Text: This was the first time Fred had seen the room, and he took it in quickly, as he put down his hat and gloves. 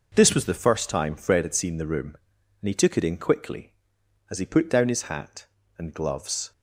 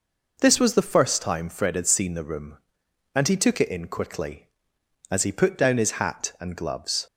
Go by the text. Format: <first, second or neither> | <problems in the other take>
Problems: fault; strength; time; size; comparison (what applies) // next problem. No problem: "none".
neither | none